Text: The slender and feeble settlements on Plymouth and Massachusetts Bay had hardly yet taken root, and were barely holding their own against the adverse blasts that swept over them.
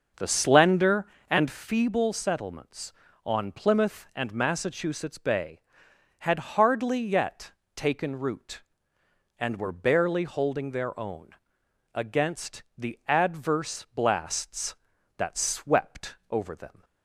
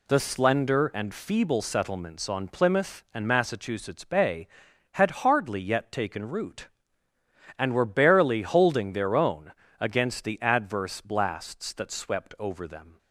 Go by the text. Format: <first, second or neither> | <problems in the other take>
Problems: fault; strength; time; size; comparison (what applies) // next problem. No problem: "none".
second | starts louder than the rest; until 1.6 s; 6.5 dB // pauses between "yet" and "taken"; slight; at 7.5 s; 0.22 s long // pauses between "own" and "against"; noticeable; at 11.3 s; 0.58 s long; slight in the second // pauses between "against" and "the"; slight; at 12.6 s; 0.16 s long // pauses between "swept" and "over"; slight; at 16.1 s; 0.16 s long